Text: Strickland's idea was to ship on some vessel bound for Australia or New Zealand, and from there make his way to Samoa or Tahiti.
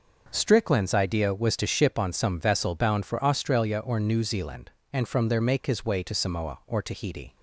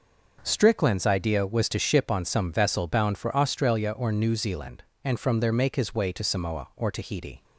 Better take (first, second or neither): neither